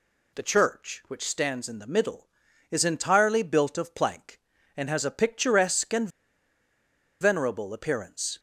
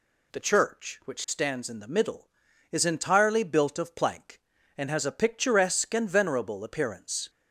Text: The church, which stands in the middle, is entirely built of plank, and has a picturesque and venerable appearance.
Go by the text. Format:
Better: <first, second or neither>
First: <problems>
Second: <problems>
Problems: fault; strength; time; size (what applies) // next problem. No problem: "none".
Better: second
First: pauses between "and" and "venerable"; at 6.0 s; 1.1 s long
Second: none